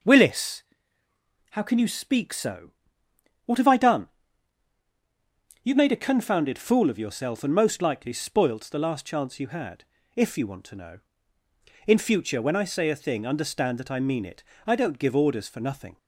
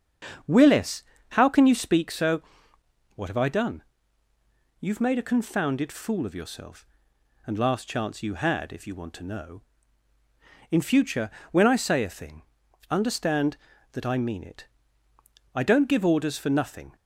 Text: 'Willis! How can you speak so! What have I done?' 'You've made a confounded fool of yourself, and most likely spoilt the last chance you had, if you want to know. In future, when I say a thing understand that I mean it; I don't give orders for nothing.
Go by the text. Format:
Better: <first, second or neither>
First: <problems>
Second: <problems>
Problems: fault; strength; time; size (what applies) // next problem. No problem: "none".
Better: first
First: none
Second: starts louder than the rest; strong; until 1.7 s; 7.5 dB // skips "most likely spoilt the"; at 7.5 s // pauses between "thing" and "understand"; noticeable; at 12.4 s; 0.46 s long